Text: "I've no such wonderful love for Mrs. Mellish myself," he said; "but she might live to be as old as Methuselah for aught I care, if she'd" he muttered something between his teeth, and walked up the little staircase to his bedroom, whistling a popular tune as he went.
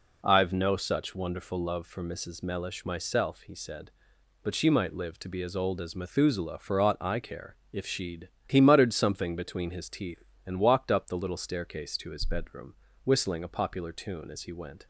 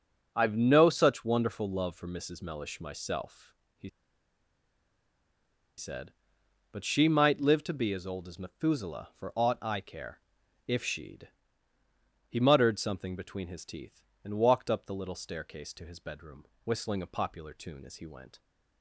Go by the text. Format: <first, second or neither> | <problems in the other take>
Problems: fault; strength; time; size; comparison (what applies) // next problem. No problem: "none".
first | pauses between "he" and "said"; strong; at 3.8 s; 1.8 s long // pauses between "she'd" and "he"; at 11.2 s; 1.0 s long; slight in the first